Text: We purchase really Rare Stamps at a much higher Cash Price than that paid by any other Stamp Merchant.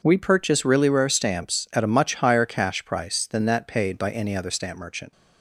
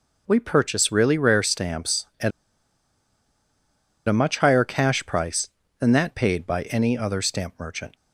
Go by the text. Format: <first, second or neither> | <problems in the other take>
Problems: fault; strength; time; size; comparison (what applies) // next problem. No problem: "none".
first | pauses between "at" and "a"; strong; at 2.3 s; 1.7 s long